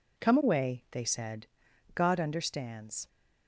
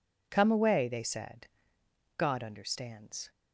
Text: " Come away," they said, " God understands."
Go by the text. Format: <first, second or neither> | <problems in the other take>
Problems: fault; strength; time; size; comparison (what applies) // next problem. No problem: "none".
neither | none